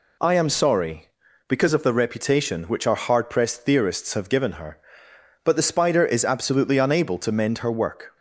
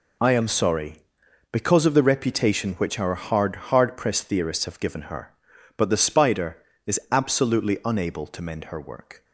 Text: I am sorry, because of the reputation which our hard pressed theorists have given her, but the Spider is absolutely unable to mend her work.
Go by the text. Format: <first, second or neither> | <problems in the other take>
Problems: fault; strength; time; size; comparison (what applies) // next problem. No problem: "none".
first | says "hard" twice; at 3.6 s